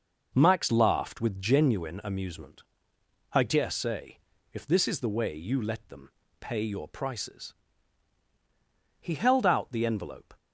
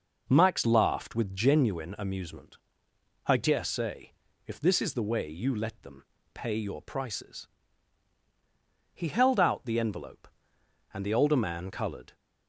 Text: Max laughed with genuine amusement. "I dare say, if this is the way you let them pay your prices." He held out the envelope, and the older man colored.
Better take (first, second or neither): second